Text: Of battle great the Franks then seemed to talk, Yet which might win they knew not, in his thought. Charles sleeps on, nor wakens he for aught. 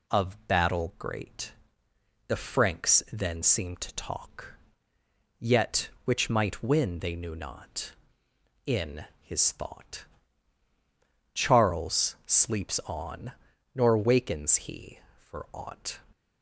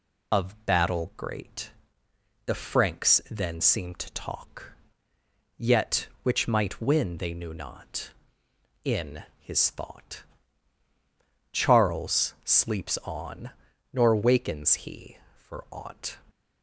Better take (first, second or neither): first